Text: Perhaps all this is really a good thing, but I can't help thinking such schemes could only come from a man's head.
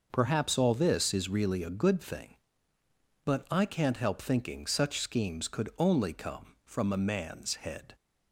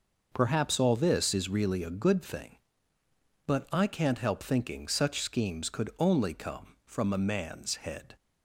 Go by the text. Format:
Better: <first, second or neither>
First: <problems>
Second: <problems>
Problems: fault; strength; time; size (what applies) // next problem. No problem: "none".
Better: neither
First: none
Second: none